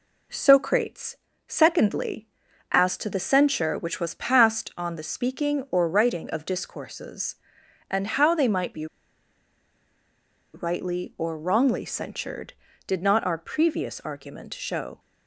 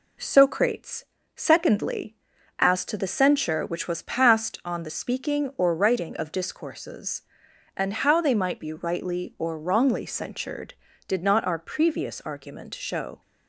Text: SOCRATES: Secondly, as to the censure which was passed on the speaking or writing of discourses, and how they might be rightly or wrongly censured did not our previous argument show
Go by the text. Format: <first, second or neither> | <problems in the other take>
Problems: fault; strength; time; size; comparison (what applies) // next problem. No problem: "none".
second | pauses between "be" and "rightly"; strong; at 8.8 s; 1.6 s long